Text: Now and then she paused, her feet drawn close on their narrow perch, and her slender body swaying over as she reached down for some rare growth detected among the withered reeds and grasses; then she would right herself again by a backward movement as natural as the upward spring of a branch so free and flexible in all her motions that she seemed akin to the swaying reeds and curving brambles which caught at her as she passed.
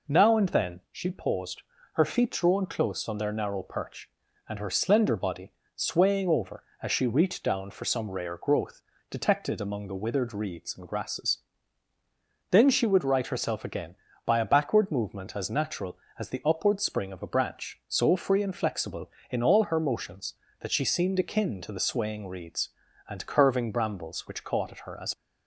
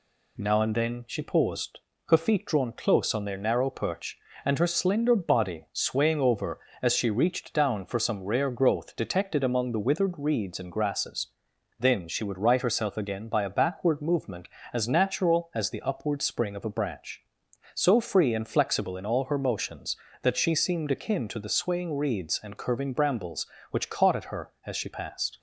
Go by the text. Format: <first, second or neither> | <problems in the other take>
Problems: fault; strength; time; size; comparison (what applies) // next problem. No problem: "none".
second | pauses between "body" and "swaying"; slight; at 5.5 s; 0.24 s long // pauses between "growth" and "detected"; slight; at 8.8 s; 0.28 s long // stops before "she passed"; at 25.1 s